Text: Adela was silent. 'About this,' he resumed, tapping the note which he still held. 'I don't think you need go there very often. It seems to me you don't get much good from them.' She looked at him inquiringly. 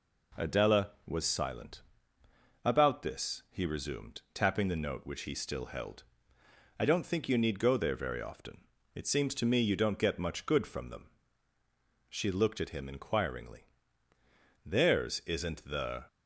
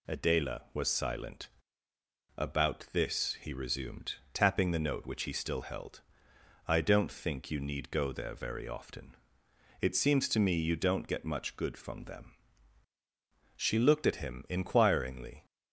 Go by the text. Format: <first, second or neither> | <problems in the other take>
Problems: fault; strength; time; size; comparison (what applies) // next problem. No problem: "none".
second | goes on to say "Theirs isn't the"; from 14.6 s on; 1.4 s long